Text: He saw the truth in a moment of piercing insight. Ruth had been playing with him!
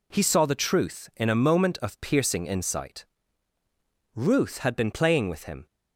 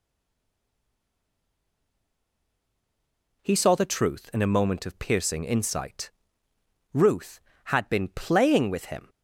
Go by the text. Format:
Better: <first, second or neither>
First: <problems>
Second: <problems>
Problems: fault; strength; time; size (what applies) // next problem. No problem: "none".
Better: first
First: none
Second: stays silent before the first word; strong; until 3.4 s; 3.4 s long